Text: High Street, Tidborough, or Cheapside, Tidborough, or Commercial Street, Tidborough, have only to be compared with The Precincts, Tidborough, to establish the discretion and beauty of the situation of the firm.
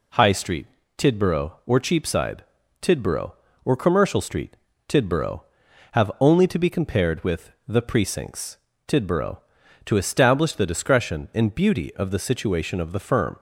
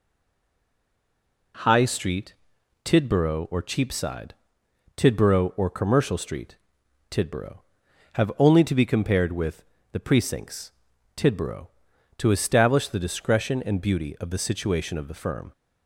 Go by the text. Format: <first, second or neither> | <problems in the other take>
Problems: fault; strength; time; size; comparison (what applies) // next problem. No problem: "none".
first | stays silent before the first word; noticeable; until 1.5 s; 1.5 s long // pauses between "with" and "The"; slight; at 9.6 s; 0.28 s long; slight in the first